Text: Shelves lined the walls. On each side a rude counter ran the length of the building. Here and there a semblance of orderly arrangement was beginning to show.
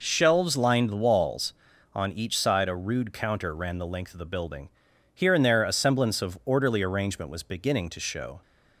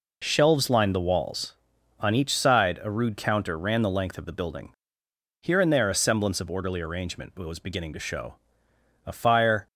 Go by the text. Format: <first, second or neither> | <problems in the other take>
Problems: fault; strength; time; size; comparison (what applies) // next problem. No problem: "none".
first | goes on to say "A fire"; noticeable; from 9.0 s on; 0.62 s long